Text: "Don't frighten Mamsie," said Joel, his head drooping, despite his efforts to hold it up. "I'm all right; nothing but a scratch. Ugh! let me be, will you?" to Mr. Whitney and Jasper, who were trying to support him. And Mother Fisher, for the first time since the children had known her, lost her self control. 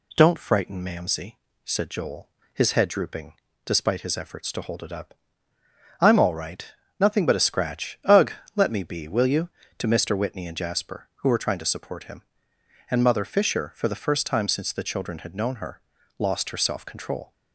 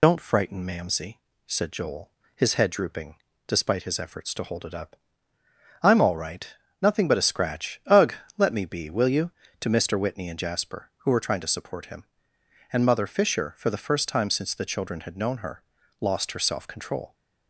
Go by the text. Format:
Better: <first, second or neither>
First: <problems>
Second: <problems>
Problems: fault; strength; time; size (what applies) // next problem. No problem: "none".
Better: first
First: none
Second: loses the start of "Don't"; at 0.0 s; 105 ms